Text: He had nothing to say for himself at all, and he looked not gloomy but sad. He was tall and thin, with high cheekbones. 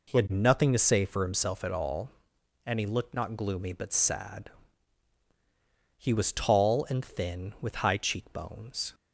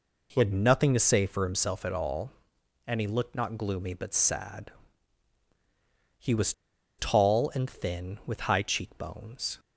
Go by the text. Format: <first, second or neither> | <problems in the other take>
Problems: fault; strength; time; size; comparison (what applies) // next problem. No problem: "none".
first | pauses between "was" and "tall"; at 6.5 s; 0.45 s long